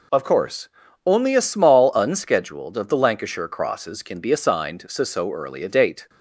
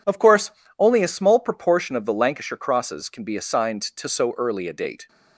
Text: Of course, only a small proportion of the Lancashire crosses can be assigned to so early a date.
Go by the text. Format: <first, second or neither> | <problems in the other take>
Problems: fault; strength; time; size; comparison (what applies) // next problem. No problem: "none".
second | says "unscheduled" for "proportion"; at 1.9 s